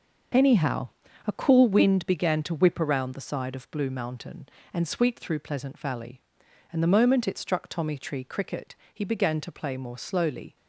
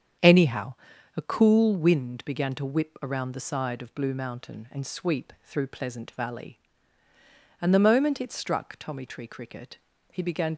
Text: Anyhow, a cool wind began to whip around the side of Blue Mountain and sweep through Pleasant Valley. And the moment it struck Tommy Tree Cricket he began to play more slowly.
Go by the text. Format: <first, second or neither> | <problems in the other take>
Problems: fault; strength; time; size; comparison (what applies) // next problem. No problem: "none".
first | starts louder than the rest; strong; until 1.6 s; 8 dB // pauses between "Cricket" and "he"; slight; at 9.7 s; 0.34 s long; slight in the first // stops before "to play more slowly"; at 10.5 s